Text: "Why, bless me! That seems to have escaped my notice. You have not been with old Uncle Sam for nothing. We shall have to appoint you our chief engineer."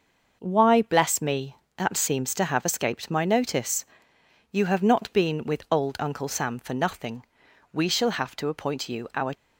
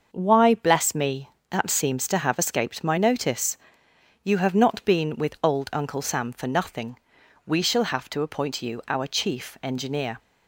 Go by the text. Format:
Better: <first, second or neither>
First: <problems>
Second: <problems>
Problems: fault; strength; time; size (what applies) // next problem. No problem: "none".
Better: second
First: starts louder than the rest; noticeable; until 1.4 s; 6 dB // stops before "chief engineer"; at 9.3 s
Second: starts louder than the rest; until 1.1 s; 6.5 dB